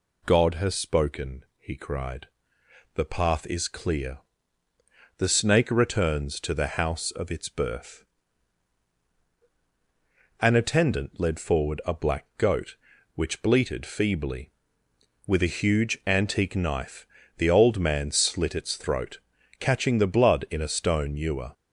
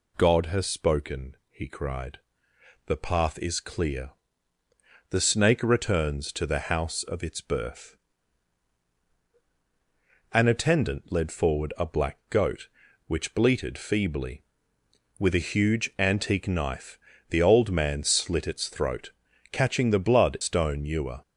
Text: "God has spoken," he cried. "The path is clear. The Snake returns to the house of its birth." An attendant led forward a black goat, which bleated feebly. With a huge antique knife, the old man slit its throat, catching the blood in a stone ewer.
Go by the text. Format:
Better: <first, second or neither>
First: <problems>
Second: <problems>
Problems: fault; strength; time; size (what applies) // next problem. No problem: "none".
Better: first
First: none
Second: skips "in a"; at 20.3 s